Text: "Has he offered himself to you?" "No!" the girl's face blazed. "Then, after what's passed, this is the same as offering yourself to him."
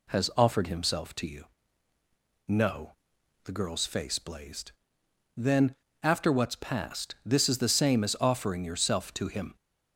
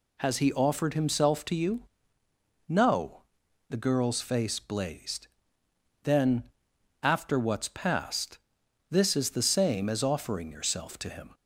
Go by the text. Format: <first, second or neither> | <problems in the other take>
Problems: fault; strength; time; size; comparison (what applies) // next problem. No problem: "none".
second | skips "he"; at 0.3 s